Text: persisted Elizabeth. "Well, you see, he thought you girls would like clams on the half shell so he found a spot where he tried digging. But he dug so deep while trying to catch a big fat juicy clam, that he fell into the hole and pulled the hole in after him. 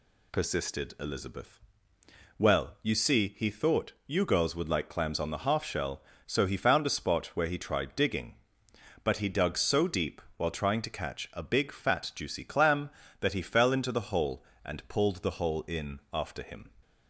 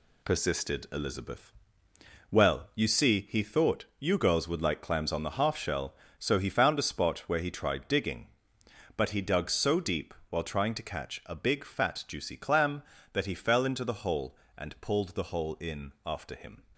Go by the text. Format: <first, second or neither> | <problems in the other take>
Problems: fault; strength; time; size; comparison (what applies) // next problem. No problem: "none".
first | gets quieter; throughout; 6.5 dB // pauses between "thought" and "you"; slight; at 3.8 s; 0.16 s long; slight in the first // pauses between "deep" and "while"; slight; at 10.1 s; 0.16 s long; slight in the first